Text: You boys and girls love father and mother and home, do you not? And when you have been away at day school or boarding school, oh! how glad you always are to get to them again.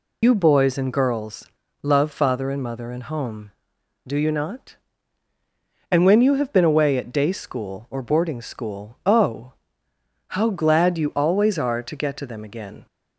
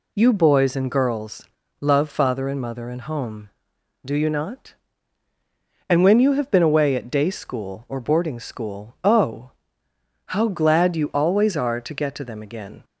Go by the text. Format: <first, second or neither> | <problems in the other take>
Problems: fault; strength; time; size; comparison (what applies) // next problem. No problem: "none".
second | loses the start of "You"; at 0.2 s; 70 ms // pauses between "girls" and "love"; slight; at 1.4 s; 0.32 s long; slight in the second